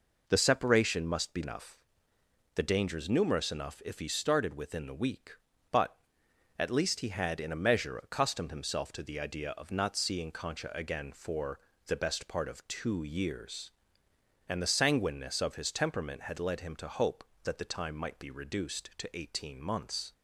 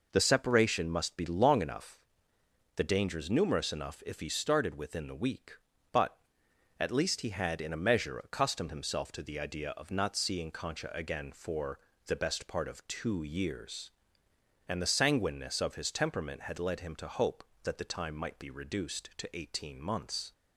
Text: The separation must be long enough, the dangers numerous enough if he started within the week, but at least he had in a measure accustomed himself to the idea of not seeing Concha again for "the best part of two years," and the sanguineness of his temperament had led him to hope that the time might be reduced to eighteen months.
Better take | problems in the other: second | skips "long"; at 1.4 s // pauses between "for" and "the"; slight; at 11.5 s; 0.28 s long; slight in the second

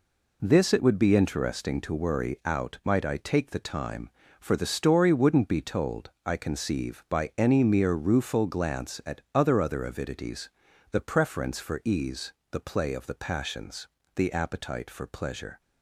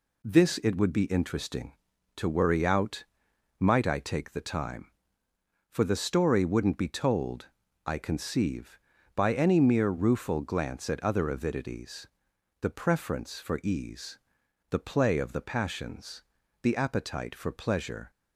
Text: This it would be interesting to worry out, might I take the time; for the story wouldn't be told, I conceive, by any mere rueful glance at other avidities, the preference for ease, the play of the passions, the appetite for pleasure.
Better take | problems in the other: second | says "other" twice; at 9.5 s

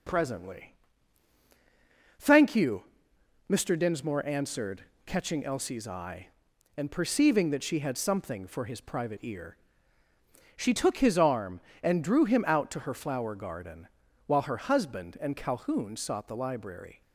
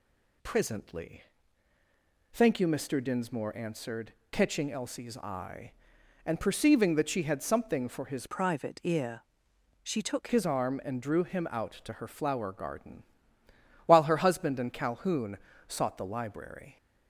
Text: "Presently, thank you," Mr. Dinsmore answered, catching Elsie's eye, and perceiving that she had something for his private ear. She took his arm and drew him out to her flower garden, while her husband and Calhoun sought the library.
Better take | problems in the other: first | changes voice from "private" to "took"; from 8.2 to 10.2 s; 2.0 s long // pauses between "Calhoun" and "sought"; slight; at 15.3 s; 0.30 s long

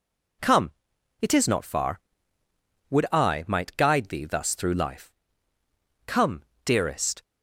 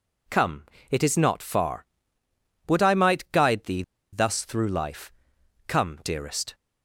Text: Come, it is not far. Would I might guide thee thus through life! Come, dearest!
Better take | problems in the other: first | pauses between "thee" and "thus"; slight; at 3.8 s; 0.30 s long

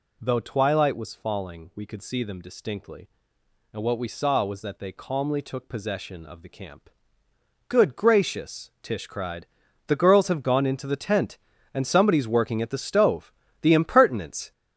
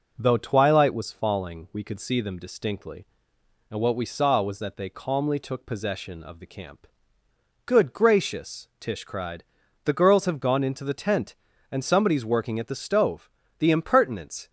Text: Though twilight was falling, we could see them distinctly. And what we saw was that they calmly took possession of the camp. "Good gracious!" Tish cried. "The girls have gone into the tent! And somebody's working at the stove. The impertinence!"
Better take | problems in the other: second | gets louder; throughout; 7 dB

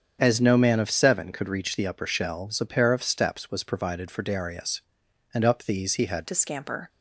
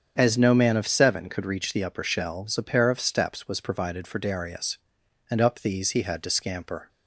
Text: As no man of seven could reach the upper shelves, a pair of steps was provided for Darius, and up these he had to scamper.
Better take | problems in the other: second | starts louder than the rest; strong; until 1.2 s; 7.5 dB; strong in the second // changes voice at "to"; from 6.2 s on; 0.6 s long

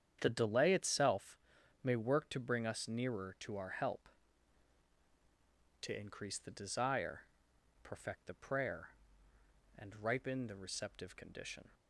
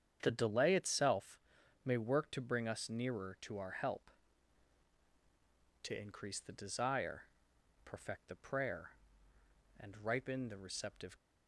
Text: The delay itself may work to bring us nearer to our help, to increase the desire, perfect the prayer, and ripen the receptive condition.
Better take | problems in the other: first | starts louder than the rest; strong; until 1.2 s; 8 dB; strong in the first // pauses between "itself" and "may"; at 1.3 s; 0.44 s long; also in the first // stops before "condition"; at 11.1 s

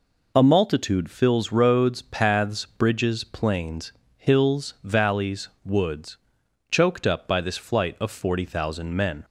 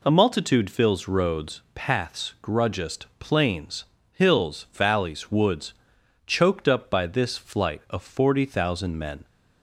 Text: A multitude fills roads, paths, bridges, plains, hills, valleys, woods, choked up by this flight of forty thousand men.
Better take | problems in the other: first | says "grudgest" for "bridges"; at 2.4 s

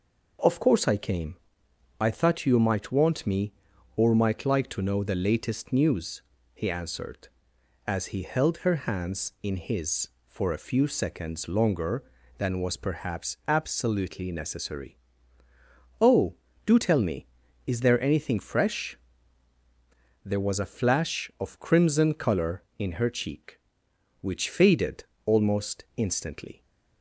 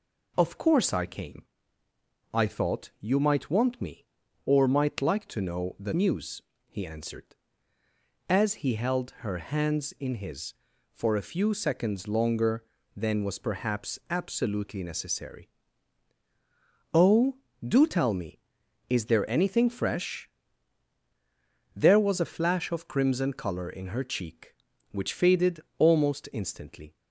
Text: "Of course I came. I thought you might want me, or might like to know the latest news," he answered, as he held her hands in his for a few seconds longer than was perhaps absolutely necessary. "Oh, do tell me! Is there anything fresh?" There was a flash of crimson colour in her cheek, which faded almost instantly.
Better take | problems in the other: first | skips "latest"; at 5.9 s // pauses between "faded" and "almost"; slight; at 25.5 s; 0.18 s long; slight in the first

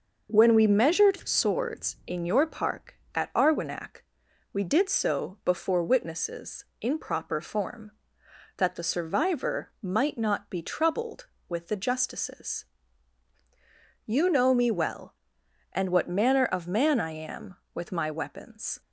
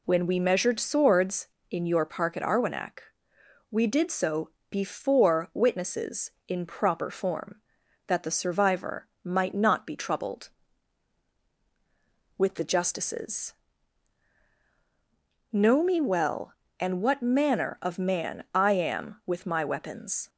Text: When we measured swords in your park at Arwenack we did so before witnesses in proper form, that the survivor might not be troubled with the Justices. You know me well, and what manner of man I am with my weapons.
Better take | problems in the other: first | pauses between "Arwenack" and "we"; noticeable; at 2.9 s; 0.72 s long; noticeable in the first // pauses between "so" and "before"; slight; at 4.5 s; 0.20 s long // pauses between "survivor" and "might"; slight; at 9.0 s; 0.16 s long // skips "You"; at 14.5 s

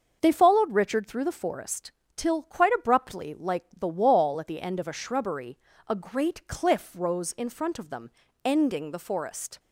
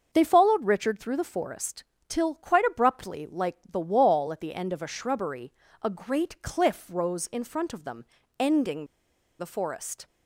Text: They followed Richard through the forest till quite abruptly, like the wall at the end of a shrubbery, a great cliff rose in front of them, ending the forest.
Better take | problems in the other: first | starts louder than the rest; until 1.1 s; 6.5 dB; also in the first // pauses between "forest" and "till"; slight; at 1.8 s; 0.24 s long; slight in the first // pauses between "ending" and "the"; noticeable; at 8.8 s; 0.55 s long

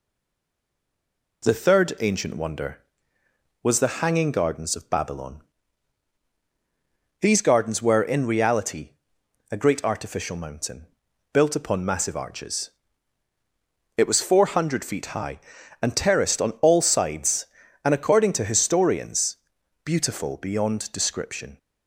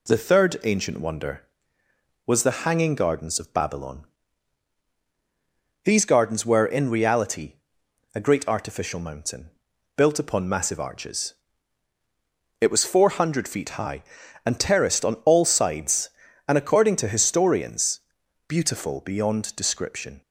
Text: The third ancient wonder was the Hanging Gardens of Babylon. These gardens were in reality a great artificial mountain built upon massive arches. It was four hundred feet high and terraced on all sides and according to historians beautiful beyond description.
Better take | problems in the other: second | stays silent before the first word; noticeable; until 1.4 s; 1.4 s long // pauses between "reality" and "a"; noticeable; at 8.9 s; 0.60 s long; noticeable in the second // pauses between "mountain" and "built"; noticeable; at 10.8 s; 0.48 s long; noticeable in the second // pauses between "historians" and "beautiful"; noticeable; at 19.3 s; 0.48 s long; noticeable in the second

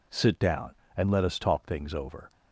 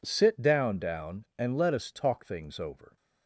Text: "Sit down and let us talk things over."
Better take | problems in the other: first | says "down" twice; at 0.7 s

